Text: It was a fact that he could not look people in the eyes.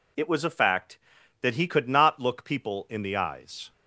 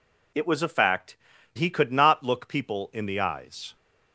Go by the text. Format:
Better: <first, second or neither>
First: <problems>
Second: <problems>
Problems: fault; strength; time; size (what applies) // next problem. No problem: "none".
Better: first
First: none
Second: skips "that"; at 1.3 s